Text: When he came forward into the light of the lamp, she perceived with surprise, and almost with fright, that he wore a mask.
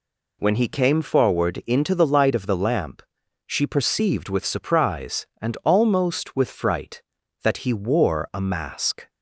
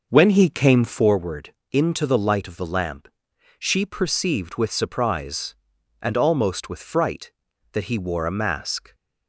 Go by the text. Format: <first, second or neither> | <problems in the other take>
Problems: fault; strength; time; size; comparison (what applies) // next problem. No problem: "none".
first | starts louder than the rest; noticeable; until 1.1 s; 6 dB // pauses between "forward" and "into"; slight; at 1.5 s; 0.18 s long